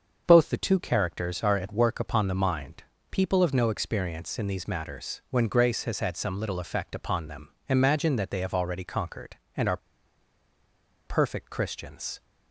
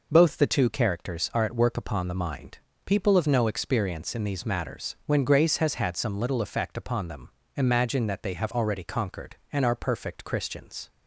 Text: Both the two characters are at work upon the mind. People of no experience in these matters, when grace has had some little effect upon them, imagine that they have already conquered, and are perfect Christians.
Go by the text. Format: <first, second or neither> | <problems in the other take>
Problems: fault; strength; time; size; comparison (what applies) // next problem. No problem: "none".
second | starts louder than the rest; until 1.2 s; 6.5 dB // pauses between "are" and "perfect"; strong; at 9.7 s; 1.2 s long